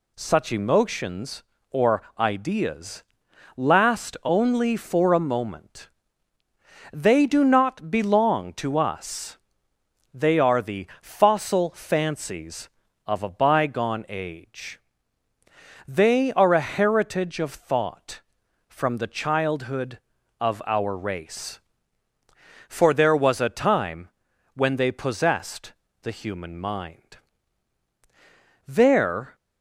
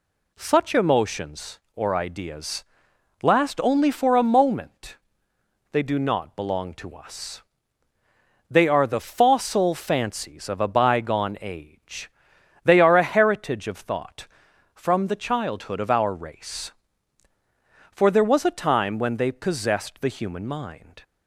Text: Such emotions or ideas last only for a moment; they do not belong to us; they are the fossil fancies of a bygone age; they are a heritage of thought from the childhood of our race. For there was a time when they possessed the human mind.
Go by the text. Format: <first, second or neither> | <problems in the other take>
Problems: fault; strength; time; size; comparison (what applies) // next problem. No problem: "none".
second | pauses between "or" and "ideas"; slight; at 2.0 s; 0.18 s long // pauses between "ideas" and "last"; noticeable; at 3.0 s; 0.54 s long; noticeable in the second // pauses between "time" and "when"; noticeable; at 24.0 s; 0.46 s long // pauses between "possessed" and "the"; slight; at 25.7 s; 0.26 s long // goes on to say "There"; noticeable; from 28.6 s on; 0.70 s long